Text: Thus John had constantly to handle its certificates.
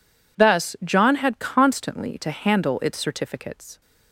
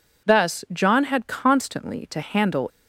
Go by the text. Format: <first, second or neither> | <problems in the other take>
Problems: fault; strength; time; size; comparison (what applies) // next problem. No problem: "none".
first | stops before "its certificates"; at 2.6 s